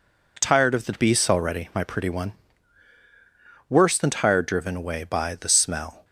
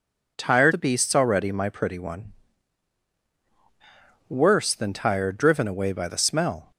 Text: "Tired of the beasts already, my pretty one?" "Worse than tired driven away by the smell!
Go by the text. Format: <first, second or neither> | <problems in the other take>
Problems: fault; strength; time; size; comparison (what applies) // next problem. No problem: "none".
first | skips "of"; at 0.7 s